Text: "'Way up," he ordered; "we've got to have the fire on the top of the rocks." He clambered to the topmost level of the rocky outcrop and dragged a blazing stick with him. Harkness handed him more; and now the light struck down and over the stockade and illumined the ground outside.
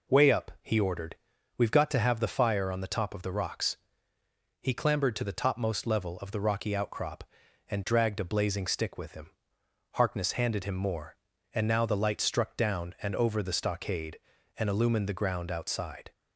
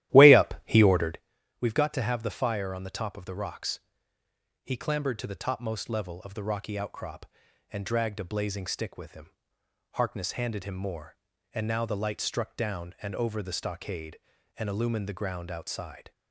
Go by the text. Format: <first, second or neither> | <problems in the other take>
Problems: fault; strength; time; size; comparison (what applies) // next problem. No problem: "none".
first | starts louder than the rest; strong; until 1.2 s; 14 dB